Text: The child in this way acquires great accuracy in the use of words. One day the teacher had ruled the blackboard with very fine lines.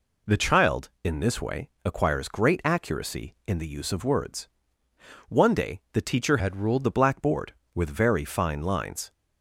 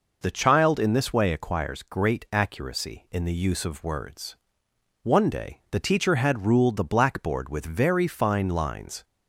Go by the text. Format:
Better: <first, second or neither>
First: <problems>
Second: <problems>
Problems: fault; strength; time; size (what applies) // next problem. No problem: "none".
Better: second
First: pauses between "way" and "acquires"; slight; at 1.6 s; 0.16 s long // changes voice from "had" to "ruled"; from 6.3 to 6.8 s; 0.5 s long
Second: none